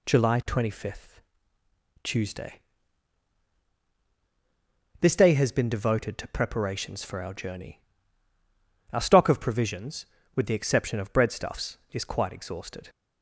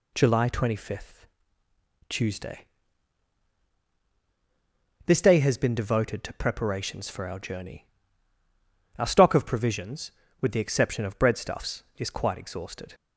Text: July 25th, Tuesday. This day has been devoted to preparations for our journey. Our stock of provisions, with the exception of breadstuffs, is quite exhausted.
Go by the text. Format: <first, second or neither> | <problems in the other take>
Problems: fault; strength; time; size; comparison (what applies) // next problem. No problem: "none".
neither | none